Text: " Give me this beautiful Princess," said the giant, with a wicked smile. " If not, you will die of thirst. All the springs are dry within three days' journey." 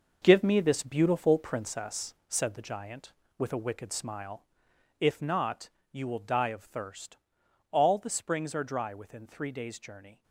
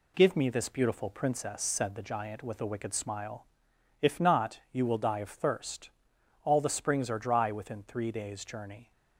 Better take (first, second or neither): second